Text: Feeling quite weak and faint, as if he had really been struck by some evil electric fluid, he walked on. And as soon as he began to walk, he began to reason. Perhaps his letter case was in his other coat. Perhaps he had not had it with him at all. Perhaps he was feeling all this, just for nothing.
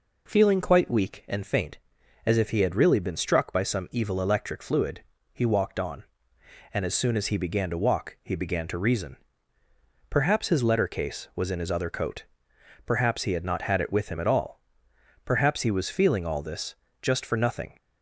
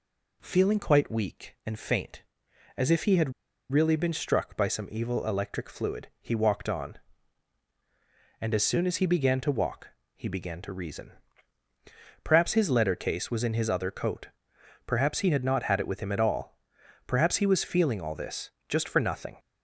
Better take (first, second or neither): first